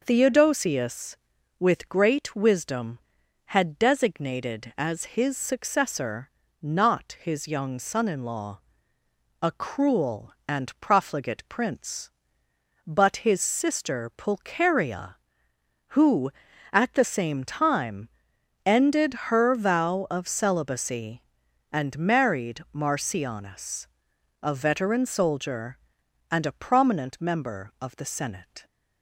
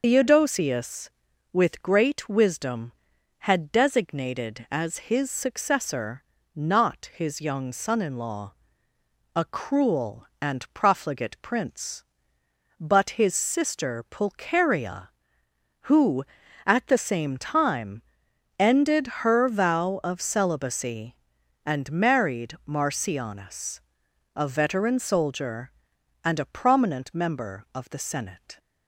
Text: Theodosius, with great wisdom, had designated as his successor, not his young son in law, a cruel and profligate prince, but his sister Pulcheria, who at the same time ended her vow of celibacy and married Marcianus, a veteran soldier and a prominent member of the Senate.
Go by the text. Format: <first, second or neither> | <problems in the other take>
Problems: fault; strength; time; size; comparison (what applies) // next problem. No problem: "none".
first | loses the start of "Theodosius"; at 0.0 s; 90 ms // pauses between "time" and "ended"; noticeable; at 18.0 s; 0.56 s long; noticeable in the first // pauses between "ended" and "her"; slight; at 19.0 s; 0.16 s long; slight in the first